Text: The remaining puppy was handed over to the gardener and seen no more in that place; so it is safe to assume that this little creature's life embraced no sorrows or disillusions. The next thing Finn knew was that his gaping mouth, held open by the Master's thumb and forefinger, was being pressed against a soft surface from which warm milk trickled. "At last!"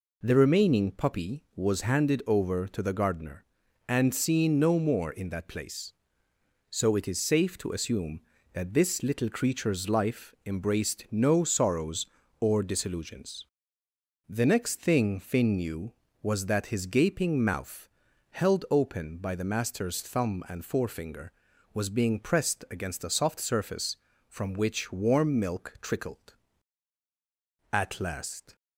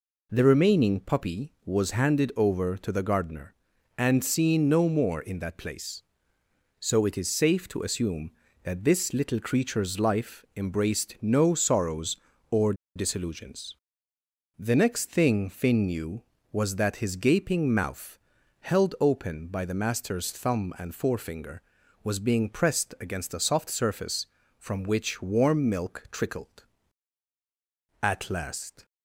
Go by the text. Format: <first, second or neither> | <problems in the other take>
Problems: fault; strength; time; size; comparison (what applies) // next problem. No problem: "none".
first | pauses between "or" and "disillusions"; slight; at 12.7 s; 0.22 s long